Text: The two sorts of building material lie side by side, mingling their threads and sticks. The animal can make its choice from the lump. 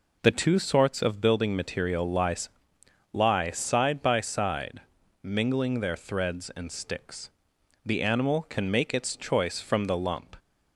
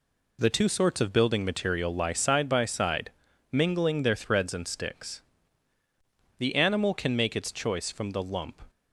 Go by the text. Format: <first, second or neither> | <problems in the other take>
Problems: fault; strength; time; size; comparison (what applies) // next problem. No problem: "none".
second | says "lie" twice; at 3.1 s